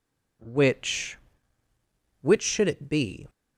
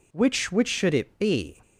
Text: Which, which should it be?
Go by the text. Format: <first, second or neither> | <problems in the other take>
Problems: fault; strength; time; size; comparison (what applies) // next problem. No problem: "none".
neither | none